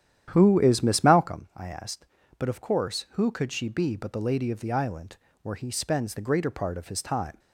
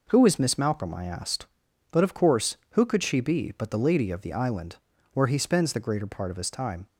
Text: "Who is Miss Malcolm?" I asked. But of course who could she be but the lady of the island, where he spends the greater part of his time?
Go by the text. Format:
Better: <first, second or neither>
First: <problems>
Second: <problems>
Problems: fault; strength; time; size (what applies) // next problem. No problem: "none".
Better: second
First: starts louder than the rest; strong; until 1.3 s; 10.5 dB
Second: none